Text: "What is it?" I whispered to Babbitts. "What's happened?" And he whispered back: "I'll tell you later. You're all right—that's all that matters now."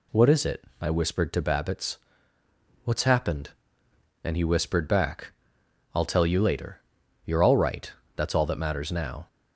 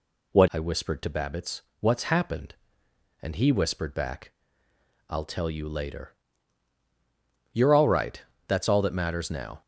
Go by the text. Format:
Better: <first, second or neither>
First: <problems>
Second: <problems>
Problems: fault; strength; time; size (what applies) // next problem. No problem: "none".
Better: first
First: none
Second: skips "is it"; at 0.4 s